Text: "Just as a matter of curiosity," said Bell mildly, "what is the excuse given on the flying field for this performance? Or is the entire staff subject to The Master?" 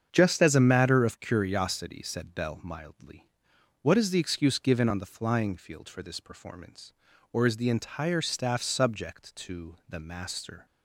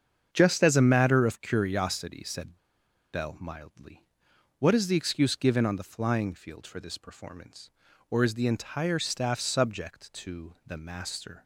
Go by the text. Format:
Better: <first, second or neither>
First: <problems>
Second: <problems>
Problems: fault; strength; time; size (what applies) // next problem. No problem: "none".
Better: first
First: starts louder than the rest; strong; until 1.1 s; 7.5 dB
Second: starts louder than the rest; strong; until 1.3 s; 7.5 dB // pauses between "said" and "Bell"; noticeable; at 2.5 s; 0.56 s long